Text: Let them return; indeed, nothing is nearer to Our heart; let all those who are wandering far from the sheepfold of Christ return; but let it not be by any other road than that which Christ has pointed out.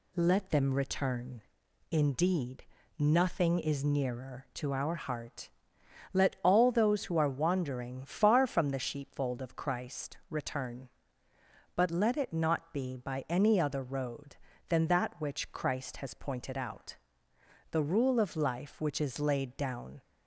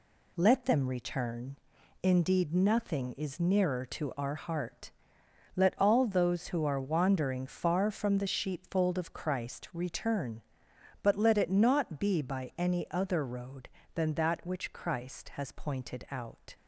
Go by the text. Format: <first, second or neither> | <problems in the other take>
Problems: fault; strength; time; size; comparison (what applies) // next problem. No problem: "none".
second | goes on to say "The rule of life which is laid down"; strong; from 17.7 s on; 2.2 s long